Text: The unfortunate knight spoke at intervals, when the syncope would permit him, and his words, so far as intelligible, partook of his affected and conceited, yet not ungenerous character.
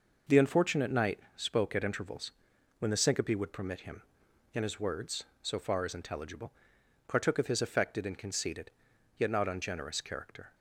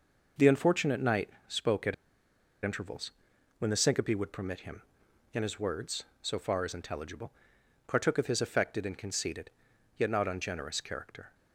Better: first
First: pauses between "knight" and "spoke"; slight; at 1.1 s; 0.16 s long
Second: pauses between "knight" and "spoke"; slight; at 1.3 s; 0.18 s long // pauses between "at" and "intervals"; noticeable; at 1.9 s; 0.69 s long

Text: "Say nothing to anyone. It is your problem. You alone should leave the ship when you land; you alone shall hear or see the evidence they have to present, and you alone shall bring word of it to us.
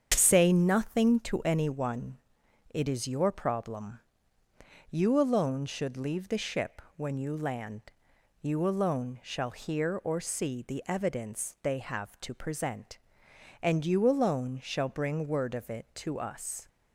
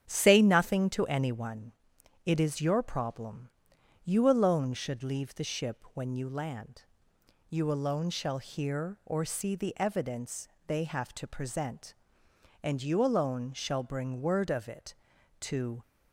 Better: first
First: starts louder than the rest; strong; until 1.1 s; 7.5 dB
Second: starts louder than the rest; strong; until 1.1 s; 8.5 dB // pauses between "evidence" and "they"; slight; at 10.4 s; 0.20 s long // stops before "us"; at 15.8 s

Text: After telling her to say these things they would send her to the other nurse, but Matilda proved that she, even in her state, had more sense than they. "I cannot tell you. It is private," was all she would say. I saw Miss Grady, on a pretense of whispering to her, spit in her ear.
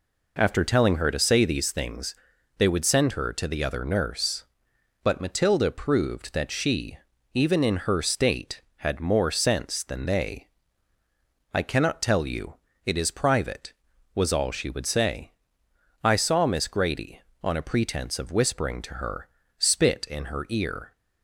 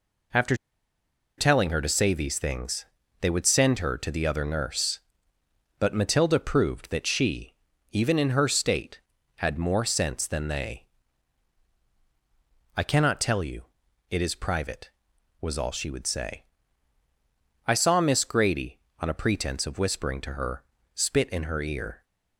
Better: first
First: pauses between "things" and "they"; at 2.1 s; 0.44 s long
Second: pauses between "After" and "telling"; noticeable; at 0.5 s; 0.82 s long // pauses between "things" and "they"; slight; at 2.8 s; 0.34 s long

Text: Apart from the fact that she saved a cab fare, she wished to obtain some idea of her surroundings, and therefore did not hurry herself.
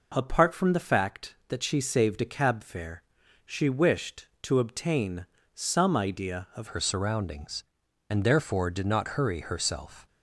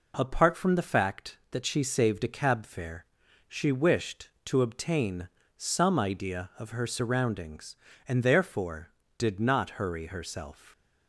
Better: second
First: pauses between "obtain" and "some"; slight; at 5.2 s; 0.30 s long // changes voice at "her"; from 6.6 s on; 3.4 s long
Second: pauses between "obtain" and "some"; slight; at 5.2 s; 0.30 s long

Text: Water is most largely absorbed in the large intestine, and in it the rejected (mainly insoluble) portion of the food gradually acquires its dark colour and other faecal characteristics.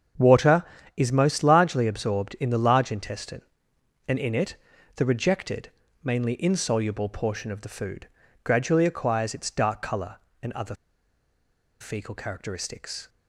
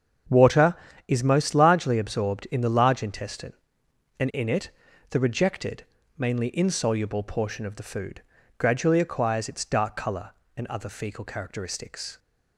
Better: second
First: starts louder than the rest; strong; until 1.5 s; 7.5 dB // pauses between "it" and "the"; at 4.5 s; 0.38 s long // pauses between "food" and "gradually"; slight; at 8.0 s; 0.34 s long // pauses between "other" and "faecal"; at 10.7 s; 1.0 s long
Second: starts louder than the rest; strong; until 1.6 s; 7.5 dB // pauses between "it" and "the"; at 4.7 s; 0.38 s long // pauses between "food" and "gradually"; slight; at 8.2 s; 0.34 s long

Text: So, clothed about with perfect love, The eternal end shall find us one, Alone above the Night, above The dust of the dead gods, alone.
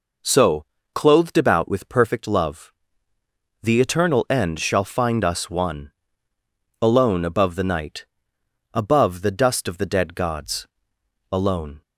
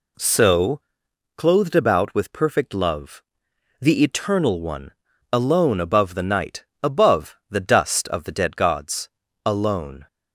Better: first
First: none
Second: skips "end shall find us"; at 4.6 s

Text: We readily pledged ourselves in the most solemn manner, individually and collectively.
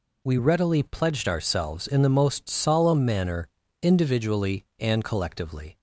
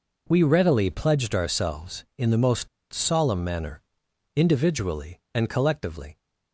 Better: first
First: none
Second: pauses between "most" and "solemn"; slight; at 2.6 s; 0.24 s long

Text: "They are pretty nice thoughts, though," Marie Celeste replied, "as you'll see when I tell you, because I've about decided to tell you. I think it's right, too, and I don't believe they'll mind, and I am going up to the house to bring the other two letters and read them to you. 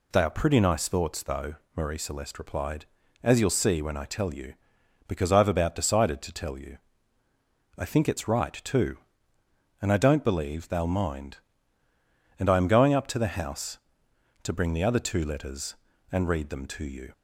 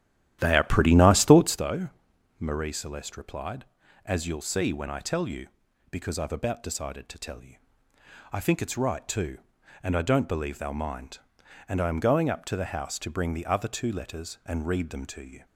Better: first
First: none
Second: starts louder than the rest; strong; until 1.6 s; 11.5 dB

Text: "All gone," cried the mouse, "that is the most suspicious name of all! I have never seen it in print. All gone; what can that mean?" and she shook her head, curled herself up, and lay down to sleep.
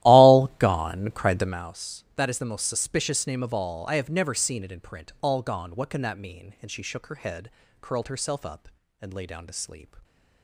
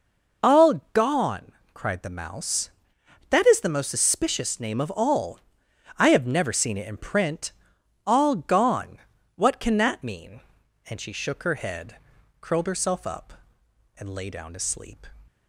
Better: second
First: starts louder than the rest; strong; until 1.7 s; 15 dB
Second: none

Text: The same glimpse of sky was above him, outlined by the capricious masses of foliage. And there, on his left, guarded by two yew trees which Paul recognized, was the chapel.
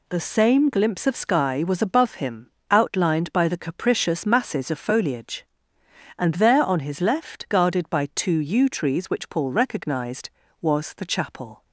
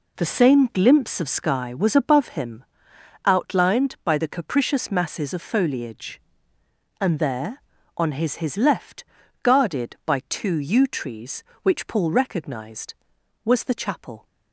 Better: first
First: none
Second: says "his" twice; at 8.3 s

